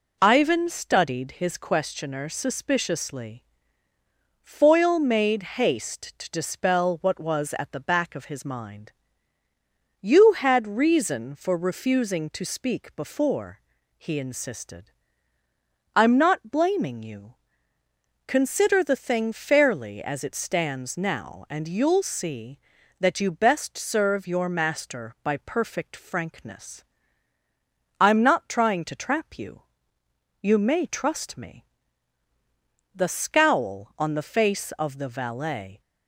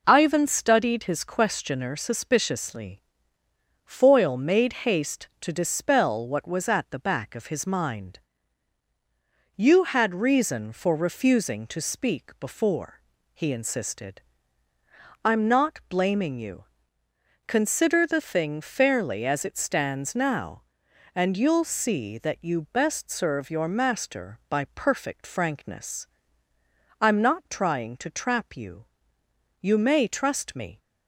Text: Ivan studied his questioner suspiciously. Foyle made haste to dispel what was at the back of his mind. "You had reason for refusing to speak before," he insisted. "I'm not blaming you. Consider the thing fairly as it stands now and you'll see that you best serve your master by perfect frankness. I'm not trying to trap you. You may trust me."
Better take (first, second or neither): second